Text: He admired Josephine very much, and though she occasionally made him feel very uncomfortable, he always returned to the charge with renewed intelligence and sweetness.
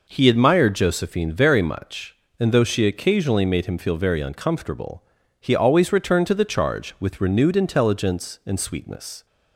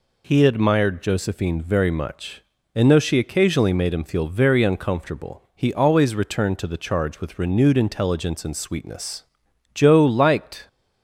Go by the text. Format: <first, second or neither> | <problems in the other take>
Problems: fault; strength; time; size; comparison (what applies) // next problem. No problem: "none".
first | goes on to say "Joe liked"; noticeable; from 9.7 s on; 0.92 s long